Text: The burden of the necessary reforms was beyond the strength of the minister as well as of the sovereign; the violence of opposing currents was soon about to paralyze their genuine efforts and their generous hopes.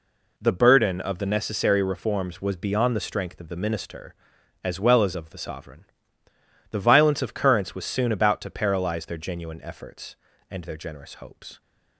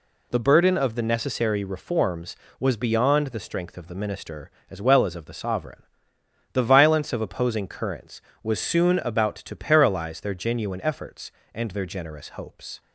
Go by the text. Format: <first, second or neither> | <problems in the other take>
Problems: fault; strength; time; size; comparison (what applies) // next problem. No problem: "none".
second | skips "opposing"; at 7.3 s